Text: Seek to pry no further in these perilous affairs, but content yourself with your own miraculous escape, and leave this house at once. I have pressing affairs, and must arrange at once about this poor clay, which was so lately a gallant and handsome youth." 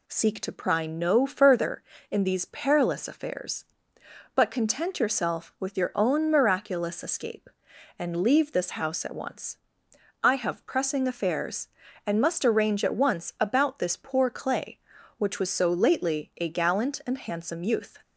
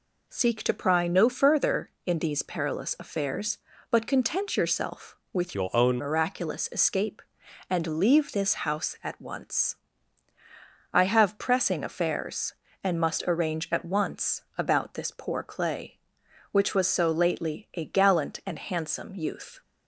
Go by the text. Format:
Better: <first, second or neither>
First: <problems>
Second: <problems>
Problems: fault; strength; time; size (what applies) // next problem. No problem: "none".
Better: first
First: none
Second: changes voice from "your" to "own"; from 5.5 to 5.9 s; 0.4 s long